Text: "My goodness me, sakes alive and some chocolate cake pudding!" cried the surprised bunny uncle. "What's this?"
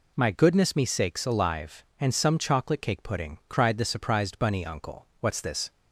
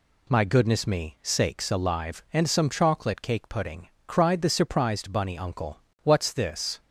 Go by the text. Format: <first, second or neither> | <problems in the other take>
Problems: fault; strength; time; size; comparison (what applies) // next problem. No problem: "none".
neither | none